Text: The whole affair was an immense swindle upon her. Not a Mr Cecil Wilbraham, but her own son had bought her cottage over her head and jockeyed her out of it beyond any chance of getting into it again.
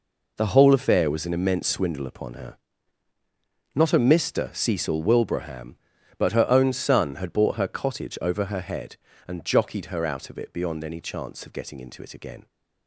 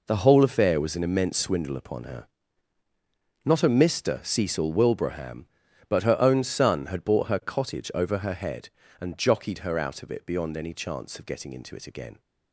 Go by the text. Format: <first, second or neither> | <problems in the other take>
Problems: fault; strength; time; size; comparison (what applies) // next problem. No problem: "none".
neither | none